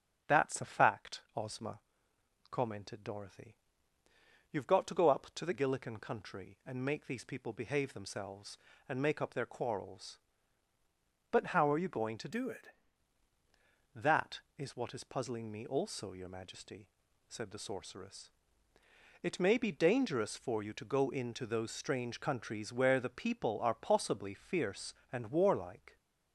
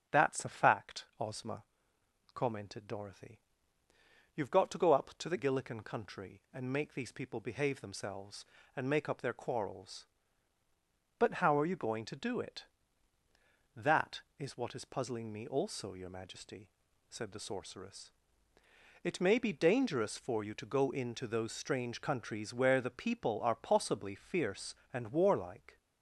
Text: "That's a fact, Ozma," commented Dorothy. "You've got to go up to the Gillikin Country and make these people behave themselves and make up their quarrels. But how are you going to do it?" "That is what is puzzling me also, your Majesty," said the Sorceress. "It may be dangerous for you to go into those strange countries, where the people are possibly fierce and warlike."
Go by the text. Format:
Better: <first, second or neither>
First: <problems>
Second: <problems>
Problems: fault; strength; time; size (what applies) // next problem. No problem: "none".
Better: second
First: starts louder than the rest; until 1.4 s; 7 dB // changes voice from "do" to "it"; from 12.3 to 12.6 s; 0.3 s long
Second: starts louder than the rest; until 1.2 s; 7 dB